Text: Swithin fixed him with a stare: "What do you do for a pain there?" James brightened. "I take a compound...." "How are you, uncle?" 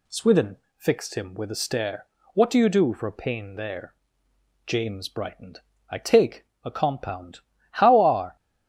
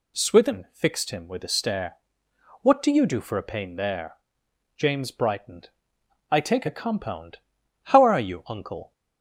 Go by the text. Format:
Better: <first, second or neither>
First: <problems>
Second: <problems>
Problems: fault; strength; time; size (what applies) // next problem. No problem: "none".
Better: second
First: pauses between "Swithin" and "fixed"; slight; at 0.5 s; 0.20 s long // pauses between "take" and "a"; slight; at 6.4 s; 0.18 s long // stops before "you uncle"; at 8.3 s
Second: none